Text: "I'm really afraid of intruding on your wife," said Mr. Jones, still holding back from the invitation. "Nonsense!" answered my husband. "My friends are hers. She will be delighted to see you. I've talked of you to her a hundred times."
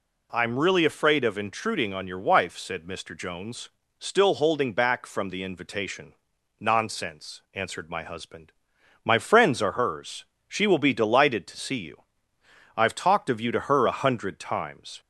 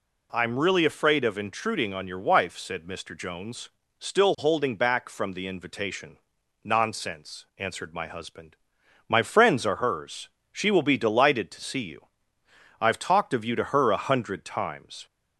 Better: neither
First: none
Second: none

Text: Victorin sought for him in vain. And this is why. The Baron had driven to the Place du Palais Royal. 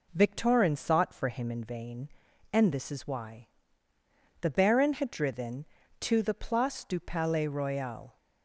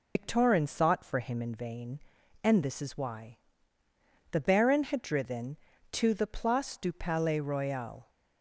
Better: first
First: none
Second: loses the start of "Victorin"; at 0.1 s; 140 ms

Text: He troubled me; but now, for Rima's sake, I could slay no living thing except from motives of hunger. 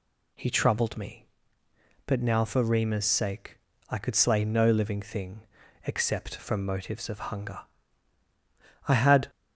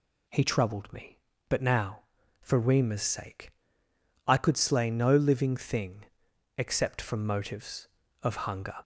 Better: second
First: pauses between "thing" and "except"; at 5.4 s; 0.44 s long // goes on to say "I had"; slight; from 8.8 s on; 0.40 s long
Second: pauses between "thing" and "except"; noticeable; at 6.0 s; 0.54 s long

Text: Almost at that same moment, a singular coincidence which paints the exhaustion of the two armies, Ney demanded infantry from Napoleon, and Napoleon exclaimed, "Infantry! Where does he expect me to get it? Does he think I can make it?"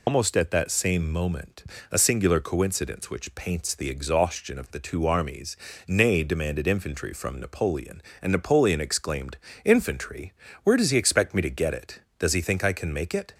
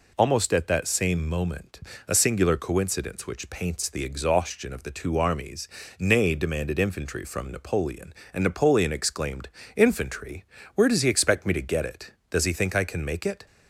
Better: second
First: loses the start of "Almost"; at 0.0 s; 80 ms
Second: none

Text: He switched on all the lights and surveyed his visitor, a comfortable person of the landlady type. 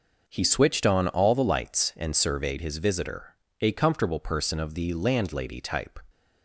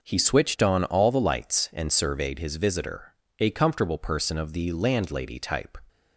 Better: neither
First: none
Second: none

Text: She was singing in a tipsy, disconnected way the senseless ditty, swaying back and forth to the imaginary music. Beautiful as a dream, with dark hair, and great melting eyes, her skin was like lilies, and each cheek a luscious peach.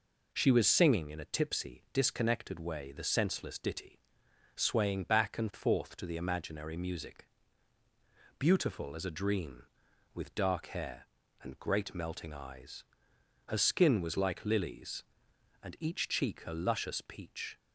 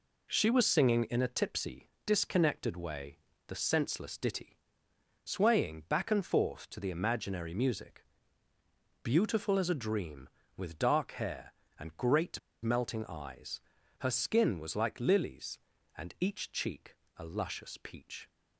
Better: first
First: none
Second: pauses between "way" and "the"; slight; at 3.1 s; 0.30 s long // pauses between "great" and "melting"; slight; at 12.3 s; 0.23 s long // pauses between "cheek" and "a"; slight; at 16.9 s; 0.20 s long

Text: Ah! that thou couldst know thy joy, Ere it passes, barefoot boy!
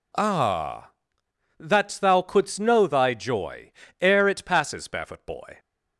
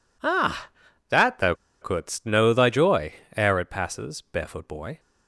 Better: first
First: none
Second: pauses between "thou" and "couldst"; slight; at 1.5 s; 0.26 s long

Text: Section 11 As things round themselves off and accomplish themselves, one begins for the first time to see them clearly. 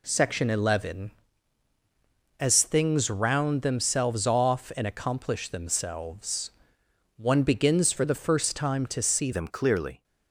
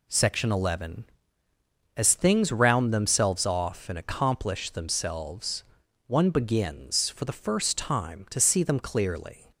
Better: second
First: changes voice at "them"; from 9.3 s on; 0.7 s long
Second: none

